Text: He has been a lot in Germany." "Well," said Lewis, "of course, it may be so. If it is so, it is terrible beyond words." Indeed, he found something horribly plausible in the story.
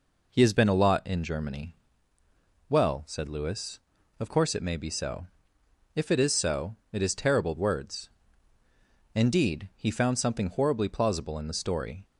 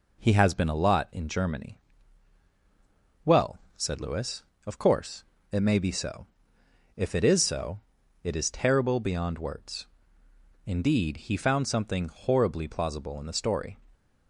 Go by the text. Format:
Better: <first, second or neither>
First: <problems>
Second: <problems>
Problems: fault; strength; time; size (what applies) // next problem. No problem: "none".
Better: second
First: skips "beyond"; at 7.5 s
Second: none